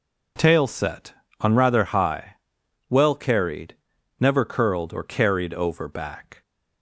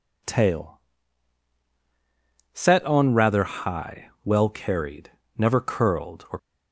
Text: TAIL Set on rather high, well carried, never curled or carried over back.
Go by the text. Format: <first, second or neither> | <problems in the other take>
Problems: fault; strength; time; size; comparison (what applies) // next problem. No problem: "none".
first | pauses between "TAIL" and "Set"; strong; at 0.7 s; 1.7 s long // stops before "carried over back"; at 6.3 s